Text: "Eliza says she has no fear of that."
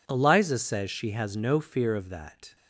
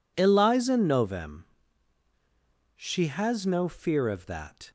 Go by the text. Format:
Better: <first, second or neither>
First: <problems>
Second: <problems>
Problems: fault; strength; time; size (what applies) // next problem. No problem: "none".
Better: first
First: none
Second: says "novem" for "says"; at 0.7 s